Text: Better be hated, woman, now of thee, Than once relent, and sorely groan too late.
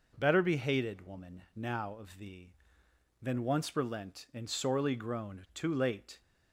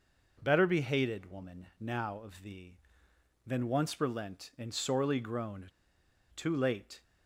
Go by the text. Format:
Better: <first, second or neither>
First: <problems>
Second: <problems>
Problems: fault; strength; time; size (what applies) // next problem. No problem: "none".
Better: first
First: none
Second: pauses between "groan" and "too"; noticeable; at 5.6 s; 0.65 s long